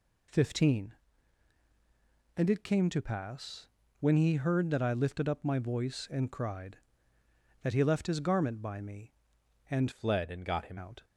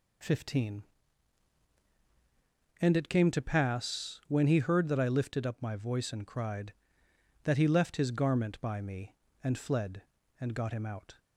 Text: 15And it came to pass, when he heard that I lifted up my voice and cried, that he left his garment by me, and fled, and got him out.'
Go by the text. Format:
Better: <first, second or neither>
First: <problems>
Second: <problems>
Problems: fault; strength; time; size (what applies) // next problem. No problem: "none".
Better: second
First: changes voice from "fled" to "him"; from 9.9 to 10.7 s; 0.8 s long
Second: none